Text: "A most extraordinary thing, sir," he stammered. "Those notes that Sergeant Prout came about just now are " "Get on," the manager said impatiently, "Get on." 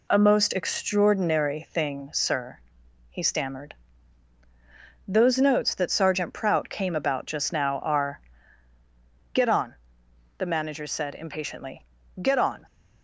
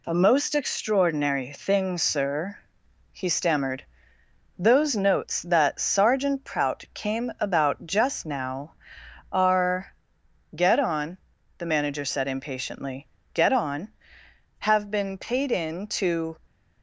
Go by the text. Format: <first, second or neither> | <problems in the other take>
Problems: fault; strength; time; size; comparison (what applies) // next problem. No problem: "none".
first | goes on to say "Have been paid in to"; strong; from 14.5 s on; 1.7 s long